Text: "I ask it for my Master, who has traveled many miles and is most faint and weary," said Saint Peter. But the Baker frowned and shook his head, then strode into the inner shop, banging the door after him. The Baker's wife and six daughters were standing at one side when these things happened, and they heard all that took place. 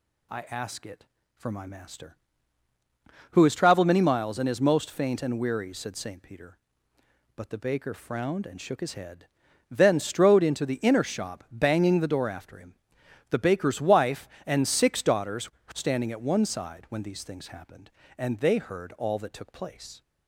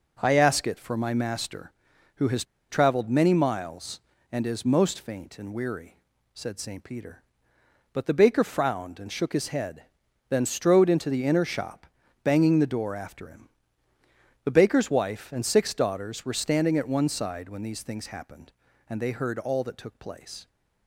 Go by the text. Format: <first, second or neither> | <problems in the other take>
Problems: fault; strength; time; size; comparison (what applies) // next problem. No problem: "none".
first | pauses between "has" and "traveled"; slight; at 2.4 s; 0.25 s long